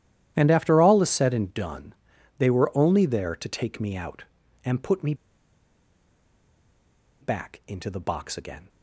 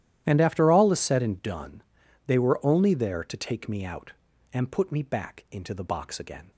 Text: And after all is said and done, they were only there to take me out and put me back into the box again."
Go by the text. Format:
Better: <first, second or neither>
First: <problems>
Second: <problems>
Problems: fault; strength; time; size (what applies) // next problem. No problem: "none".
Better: second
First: starts louder than the rest; strong; until 1.3 s; 12 dB // pauses between "me" and "back"; strong; at 5.1 s; 2.0 s long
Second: starts louder than the rest; strong; until 1.2 s; 12 dB